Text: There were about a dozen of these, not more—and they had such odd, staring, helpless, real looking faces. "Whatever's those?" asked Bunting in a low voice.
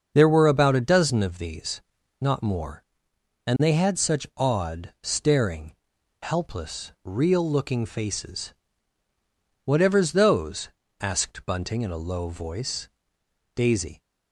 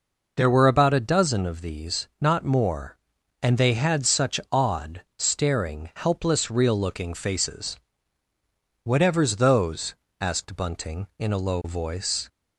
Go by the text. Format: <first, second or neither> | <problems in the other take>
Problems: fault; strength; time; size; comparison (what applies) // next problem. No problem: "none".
second | starts louder than the rest; until 1.1 s; 6.5 dB // goes on to say "Daisy"; slight; from 13.5 s on; 0.46 s long